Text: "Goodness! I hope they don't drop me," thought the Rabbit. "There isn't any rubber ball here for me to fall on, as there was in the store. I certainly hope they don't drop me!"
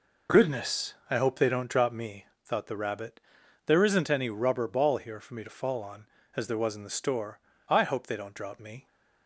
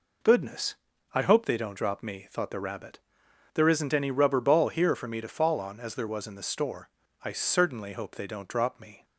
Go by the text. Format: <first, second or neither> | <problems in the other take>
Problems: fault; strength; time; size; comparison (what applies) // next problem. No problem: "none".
second | skips "certainly"; at 7.8 s